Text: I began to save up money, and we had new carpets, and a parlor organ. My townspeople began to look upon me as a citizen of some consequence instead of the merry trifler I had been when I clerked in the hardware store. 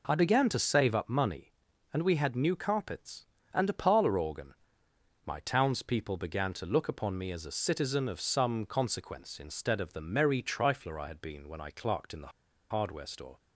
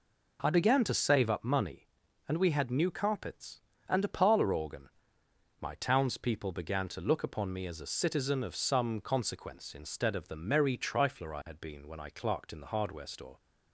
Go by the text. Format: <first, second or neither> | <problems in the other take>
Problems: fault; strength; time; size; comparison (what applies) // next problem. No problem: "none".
second | pauses between "the" and "hardware"; at 12.3 s; 0.41 s long